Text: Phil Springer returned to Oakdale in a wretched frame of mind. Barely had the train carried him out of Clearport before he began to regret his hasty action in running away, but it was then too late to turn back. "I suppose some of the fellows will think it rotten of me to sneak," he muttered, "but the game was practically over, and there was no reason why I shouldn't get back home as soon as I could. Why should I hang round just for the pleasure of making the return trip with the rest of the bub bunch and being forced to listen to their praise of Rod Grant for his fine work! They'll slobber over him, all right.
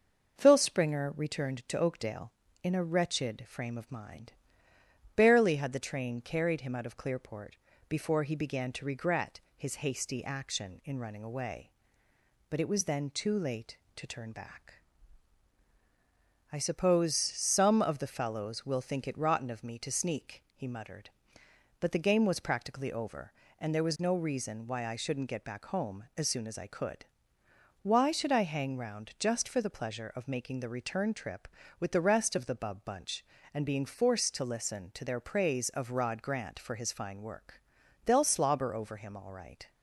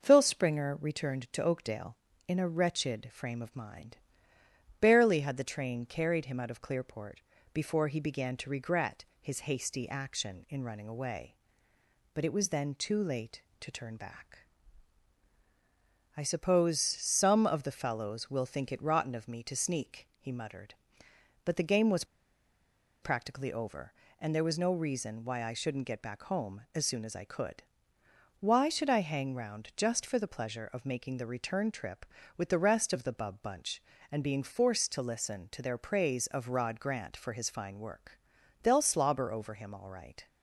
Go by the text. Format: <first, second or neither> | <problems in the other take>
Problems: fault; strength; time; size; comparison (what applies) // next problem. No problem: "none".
first | pauses between "Clearport" and "before"; slight; at 7.1 s; 0.34 s long; slight in the first // pauses between "regret" and "his"; slight; at 9.0 s; 0.18 s long; slight in the first // pauses between "was" and "practically"; at 22.0 s; 0.98 s long